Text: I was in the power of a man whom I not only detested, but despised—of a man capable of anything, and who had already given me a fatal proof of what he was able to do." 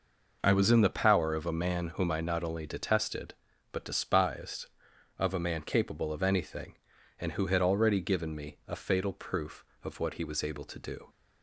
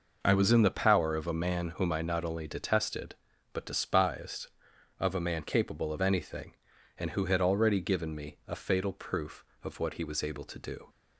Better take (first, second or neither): neither